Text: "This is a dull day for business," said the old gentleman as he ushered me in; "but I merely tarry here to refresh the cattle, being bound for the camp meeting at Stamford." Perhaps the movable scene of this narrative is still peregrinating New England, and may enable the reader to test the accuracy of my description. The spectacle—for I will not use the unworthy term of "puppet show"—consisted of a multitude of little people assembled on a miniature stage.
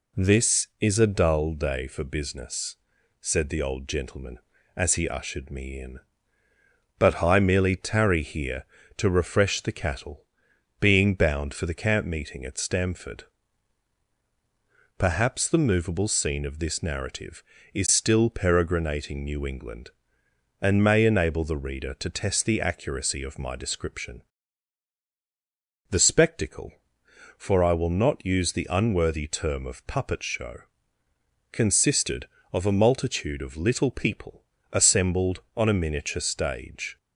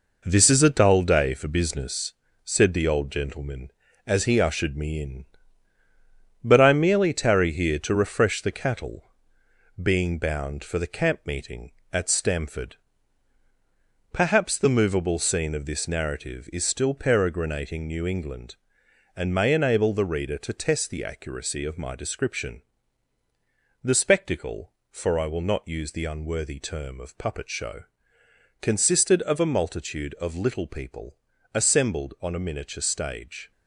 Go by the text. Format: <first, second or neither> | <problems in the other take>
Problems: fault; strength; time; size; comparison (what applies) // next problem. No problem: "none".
first | gets quieter; throughout; 7 dB // pauses between "people" and "assembled"; slight; at 31.1 s; 0.36 s long; slight in the first